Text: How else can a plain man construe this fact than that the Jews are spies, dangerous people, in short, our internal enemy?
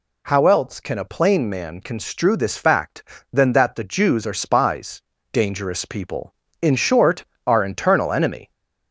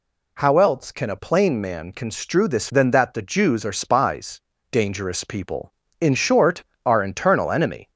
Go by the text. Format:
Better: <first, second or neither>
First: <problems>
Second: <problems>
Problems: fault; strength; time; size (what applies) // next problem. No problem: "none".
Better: first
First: none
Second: skips "fact"; at 2.6 s